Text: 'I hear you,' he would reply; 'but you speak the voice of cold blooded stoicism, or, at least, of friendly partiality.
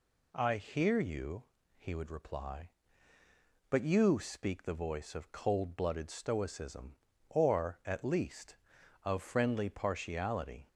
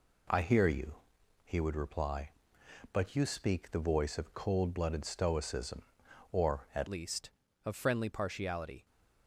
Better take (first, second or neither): first